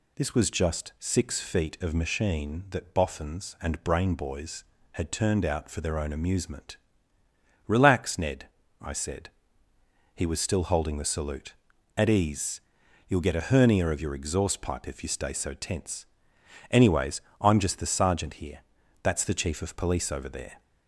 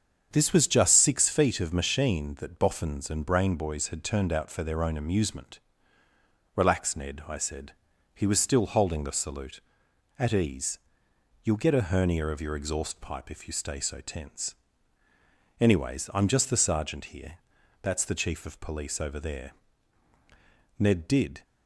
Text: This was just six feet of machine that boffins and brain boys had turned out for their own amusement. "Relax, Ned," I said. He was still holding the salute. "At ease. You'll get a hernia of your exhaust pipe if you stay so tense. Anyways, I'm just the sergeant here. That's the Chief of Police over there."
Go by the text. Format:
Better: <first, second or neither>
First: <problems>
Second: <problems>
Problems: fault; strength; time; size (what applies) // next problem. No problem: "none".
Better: first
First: none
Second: starts louder than the rest; until 1.3 s; 6.5 dB // goes on to say "Ned did"; noticeable; from 20.7 s on; 0.64 s long